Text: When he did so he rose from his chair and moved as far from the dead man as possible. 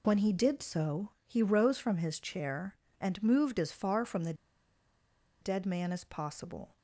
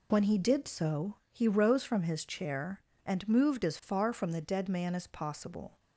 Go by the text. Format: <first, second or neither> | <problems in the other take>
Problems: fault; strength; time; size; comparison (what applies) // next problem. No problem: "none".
second | pauses between "so" and "he"; slight; at 1.0 s; 0.16 s long; slight in the second // pauses between "the" and "dead"; at 4.3 s; 1.0 s long